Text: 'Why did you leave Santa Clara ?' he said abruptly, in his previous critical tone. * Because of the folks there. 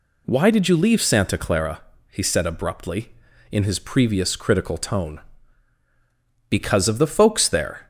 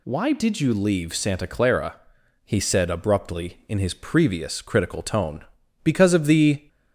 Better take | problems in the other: first | stops before "folks there"; at 6.6 s

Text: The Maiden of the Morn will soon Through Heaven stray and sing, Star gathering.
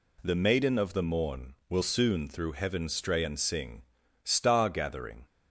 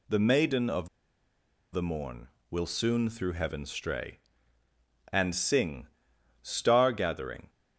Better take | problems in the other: first | pauses between "of" and "the"; noticeable; at 0.8 s; 0.84 s long

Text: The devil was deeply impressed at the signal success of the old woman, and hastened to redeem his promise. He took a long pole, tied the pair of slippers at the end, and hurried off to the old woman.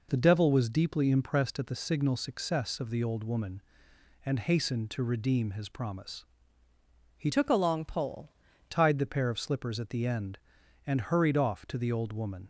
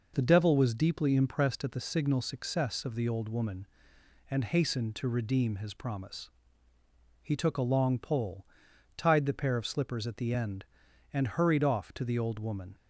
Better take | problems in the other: second | changes voice from "took" to "pole"; from 7.3 to 8.2 s; 0.9 s long

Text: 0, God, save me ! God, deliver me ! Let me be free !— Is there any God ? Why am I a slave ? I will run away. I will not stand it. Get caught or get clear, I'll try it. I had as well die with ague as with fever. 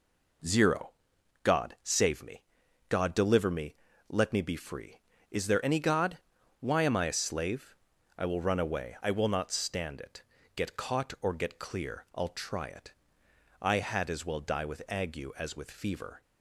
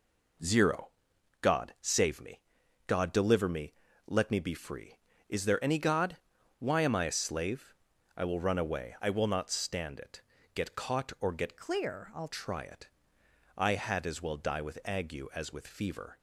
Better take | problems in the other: first | changes voice from "clear" to "I'll"; from 11.5 to 12.2 s; 0.7 s long

